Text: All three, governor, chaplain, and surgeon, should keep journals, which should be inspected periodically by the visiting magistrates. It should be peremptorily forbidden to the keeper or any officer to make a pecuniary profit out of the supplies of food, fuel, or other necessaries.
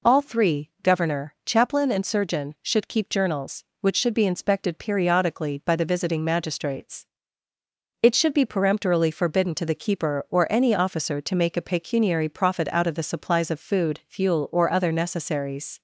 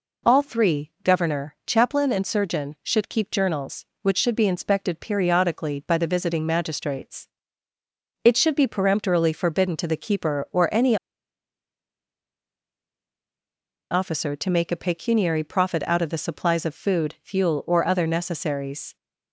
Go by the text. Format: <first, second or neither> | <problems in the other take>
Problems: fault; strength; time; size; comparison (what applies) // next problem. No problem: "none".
first | pauses between "any" and "officer"; strong; at 10.9 s; 2.9 s long